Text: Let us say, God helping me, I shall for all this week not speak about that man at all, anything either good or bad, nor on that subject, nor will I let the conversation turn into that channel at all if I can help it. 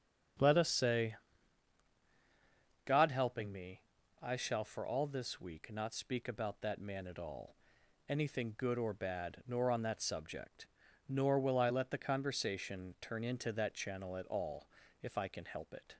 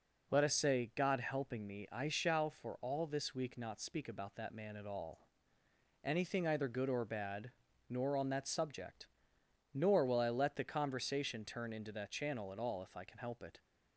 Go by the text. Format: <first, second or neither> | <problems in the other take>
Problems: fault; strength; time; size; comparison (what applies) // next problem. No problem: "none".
second | starts louder than the rest; strong; until 3.1 s; 8.5 dB // skips "either"; at 8.5 s // pauses between "all" and "if"; slight; at 14.6 s; 0.34 s long